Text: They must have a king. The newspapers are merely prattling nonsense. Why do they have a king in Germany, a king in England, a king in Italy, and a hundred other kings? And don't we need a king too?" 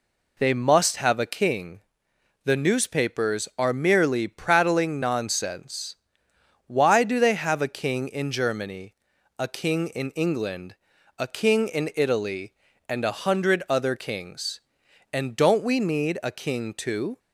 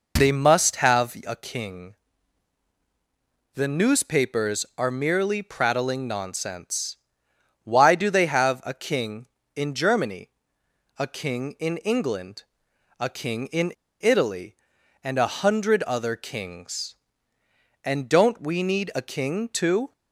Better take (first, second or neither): first